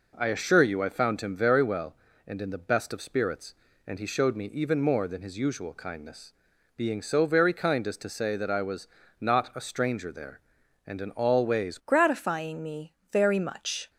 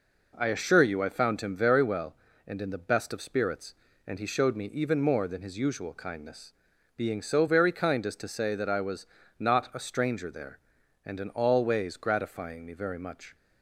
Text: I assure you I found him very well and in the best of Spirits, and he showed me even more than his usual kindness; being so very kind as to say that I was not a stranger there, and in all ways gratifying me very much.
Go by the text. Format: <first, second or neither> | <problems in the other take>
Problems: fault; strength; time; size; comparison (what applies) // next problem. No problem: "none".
second | pauses between "was" and "not"; slight; at 8.8 s; 0.34 s long; slight in the second // changes voice at "gratifying"; from 11.8 s on; 2.0 s long // pauses between "me" and "very"; slight; at 12.9 s; 0.16 s long